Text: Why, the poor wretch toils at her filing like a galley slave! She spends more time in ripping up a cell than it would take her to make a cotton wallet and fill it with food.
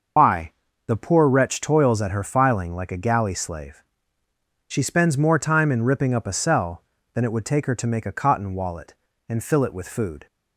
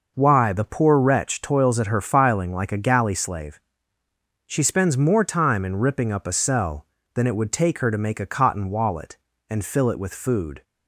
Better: second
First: loses the start of "Why"; at 0.1 s; 120 ms // starts louder than the rest; until 1.5 s; 6.5 dB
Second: none

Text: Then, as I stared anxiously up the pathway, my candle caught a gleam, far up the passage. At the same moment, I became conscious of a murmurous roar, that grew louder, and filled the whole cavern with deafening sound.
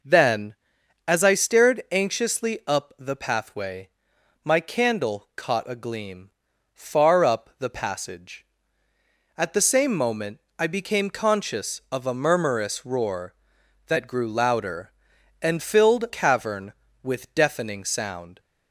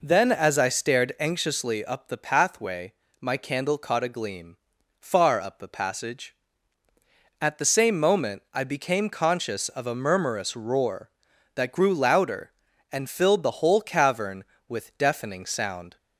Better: second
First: skips "the whole"; at 16.0 s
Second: none

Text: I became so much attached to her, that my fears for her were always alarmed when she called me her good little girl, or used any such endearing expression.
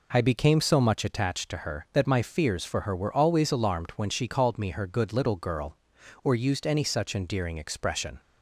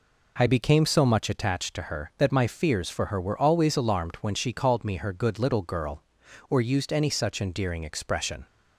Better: neither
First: none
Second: none

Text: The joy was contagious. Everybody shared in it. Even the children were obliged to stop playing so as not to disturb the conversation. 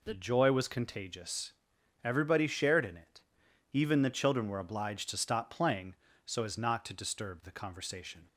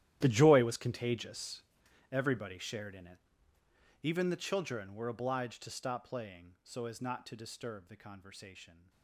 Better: first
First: none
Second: gets quieter; strong; throughout; 18.5 dB

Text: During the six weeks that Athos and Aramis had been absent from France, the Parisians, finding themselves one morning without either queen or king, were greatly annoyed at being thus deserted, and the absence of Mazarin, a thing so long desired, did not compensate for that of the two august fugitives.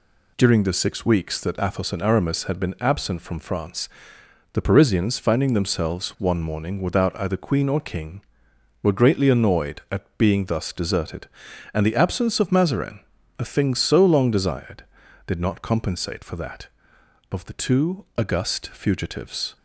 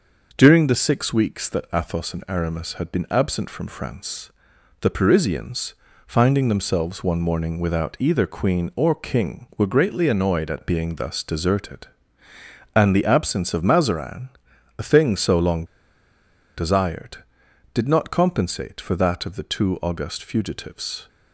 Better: first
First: none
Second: pauses between "long" and "desired"; noticeable; at 15.6 s; 0.92 s long

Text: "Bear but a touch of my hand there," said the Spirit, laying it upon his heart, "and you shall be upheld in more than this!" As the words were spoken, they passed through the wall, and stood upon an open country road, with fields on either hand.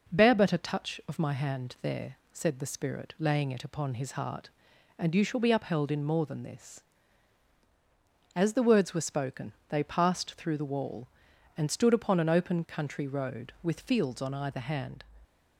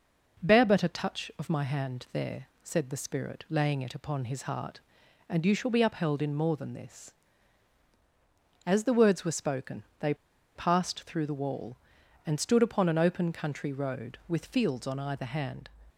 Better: first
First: none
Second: pauses between "they" and "passed"; at 10.1 s; 0.41 s long

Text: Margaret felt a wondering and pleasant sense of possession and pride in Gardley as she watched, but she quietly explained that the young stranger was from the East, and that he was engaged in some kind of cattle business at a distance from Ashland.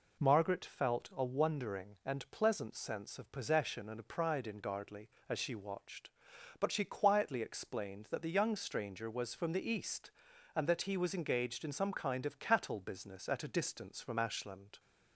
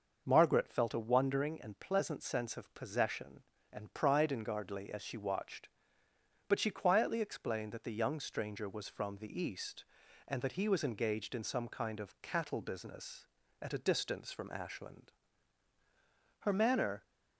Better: first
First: none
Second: starts louder than the rest; until 1.2 s; 6 dB // goes on to say "Her manner"; noticeable; from 16.3 s on; 0.64 s long

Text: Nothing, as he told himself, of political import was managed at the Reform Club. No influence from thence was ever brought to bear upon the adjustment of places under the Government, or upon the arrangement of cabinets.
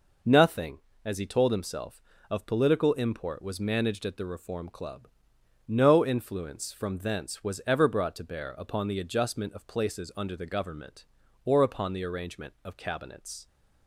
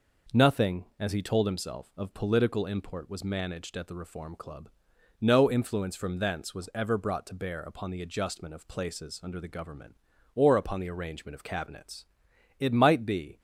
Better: first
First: none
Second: goes on to say "It might be"; noticeable; from 12.5 s on; 0.80 s long

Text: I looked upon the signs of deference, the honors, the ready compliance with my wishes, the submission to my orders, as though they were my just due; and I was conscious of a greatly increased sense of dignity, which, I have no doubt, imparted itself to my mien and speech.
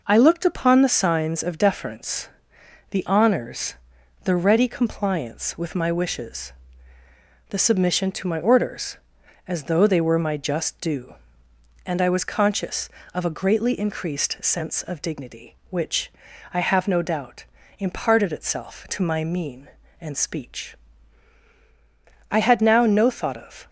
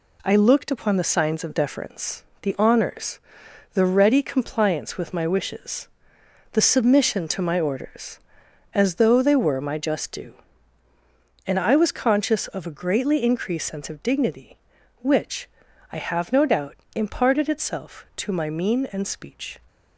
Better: second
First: goes on to say "I had now no thought of"; from 22.2 s on; 1.4 s long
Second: none

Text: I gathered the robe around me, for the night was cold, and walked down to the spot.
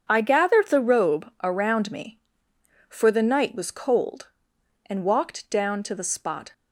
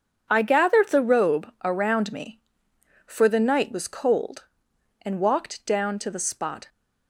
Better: neither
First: starts louder than the rest; until 1.0 s; 7 dB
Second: starts louder than the rest; strong; until 1.3 s; 7 dB

